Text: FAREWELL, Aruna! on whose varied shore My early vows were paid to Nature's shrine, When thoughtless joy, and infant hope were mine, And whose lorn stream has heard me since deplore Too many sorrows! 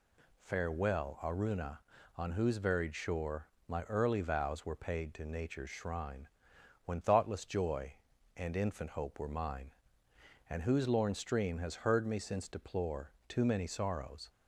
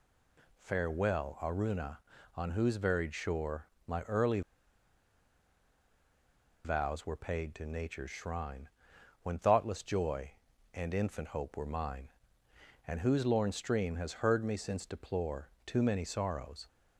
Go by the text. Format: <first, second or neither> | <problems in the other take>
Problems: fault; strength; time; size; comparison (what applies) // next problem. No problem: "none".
first | pauses between "shore" and "My"; slight; at 3.6 s; 0.20 s long; slight in the first // pauses between "early" and "vows"; strong; at 4.4 s; 2.2 s long // pauses between "deplore" and "Too"; slight; at 15.5 s; 0.16 s long; slight in the first